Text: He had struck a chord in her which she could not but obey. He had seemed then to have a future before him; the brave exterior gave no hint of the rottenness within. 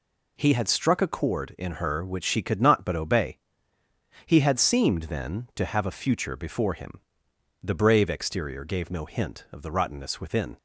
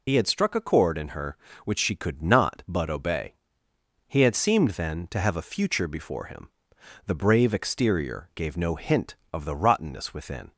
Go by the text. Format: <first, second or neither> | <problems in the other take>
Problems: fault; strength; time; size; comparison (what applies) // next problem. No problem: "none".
first | loses the start of "He"; at 0.0 s; 85 ms